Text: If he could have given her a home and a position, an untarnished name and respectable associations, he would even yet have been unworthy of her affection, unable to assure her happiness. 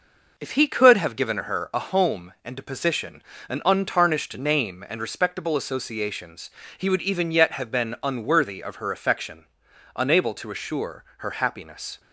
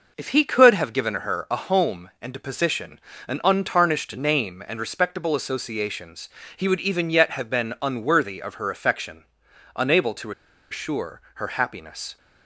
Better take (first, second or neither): first